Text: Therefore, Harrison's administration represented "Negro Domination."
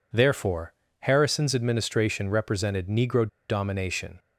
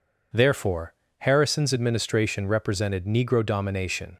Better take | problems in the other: second | pauses between "Negro" and "Domination"; slight; at 3.2 s; 0.22 s long

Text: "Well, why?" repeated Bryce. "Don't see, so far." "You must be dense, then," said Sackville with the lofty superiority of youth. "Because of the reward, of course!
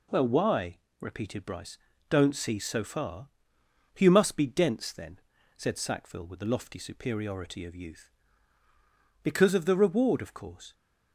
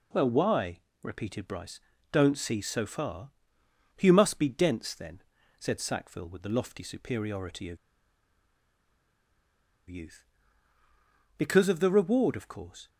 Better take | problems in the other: first | pauses between "of" and "youth"; strong; at 7.7 s; 2.1 s long

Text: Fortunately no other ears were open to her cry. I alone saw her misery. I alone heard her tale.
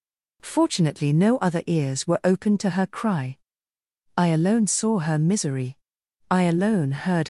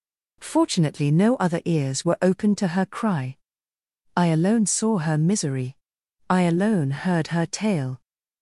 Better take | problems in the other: second | stops before "her tale"; at 7.2 s

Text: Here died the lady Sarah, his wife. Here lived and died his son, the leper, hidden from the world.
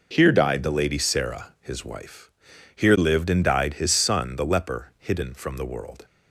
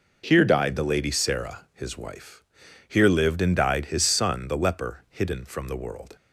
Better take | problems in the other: neither | none

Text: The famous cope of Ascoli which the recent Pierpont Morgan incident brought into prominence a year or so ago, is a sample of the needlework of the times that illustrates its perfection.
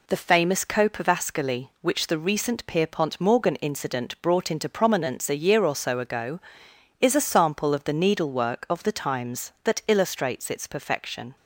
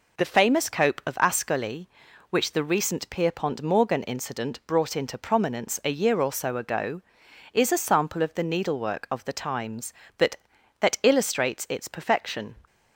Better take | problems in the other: first | says "that" twice; at 10.7 s

